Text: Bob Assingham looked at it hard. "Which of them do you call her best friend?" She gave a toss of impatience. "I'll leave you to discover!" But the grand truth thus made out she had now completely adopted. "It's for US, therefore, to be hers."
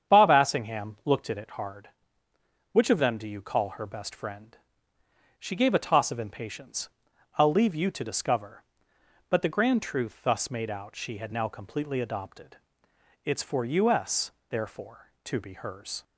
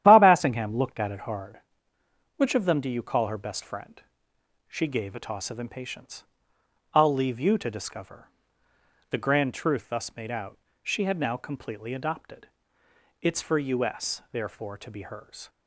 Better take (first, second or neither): first